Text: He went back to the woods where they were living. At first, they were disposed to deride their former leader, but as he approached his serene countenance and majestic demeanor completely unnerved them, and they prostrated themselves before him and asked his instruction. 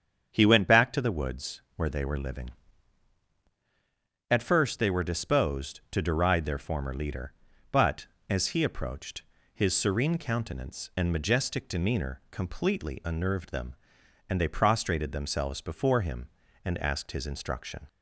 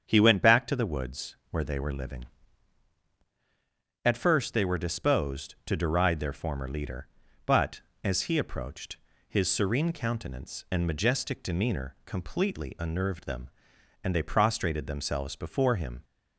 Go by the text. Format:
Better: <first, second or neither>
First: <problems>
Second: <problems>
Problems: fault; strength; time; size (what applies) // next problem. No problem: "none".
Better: first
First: starts louder than the rest; strong; until 1.3 s; 7.5 dB // pauses between "woods" and "where"; slight; at 1.5 s; 0.16 s long // pauses between "approached" and "his"; slight; at 9.2 s; 0.30 s long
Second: starts louder than the rest; strong; until 1.0 s; 7.5 dB // pauses between "woods" and "where"; slight; at 1.3 s; 0.16 s long // pauses between "approached" and "his"; slight; at 8.9 s; 0.30 s long // stops before "and asked his instruction"; at 16.0 s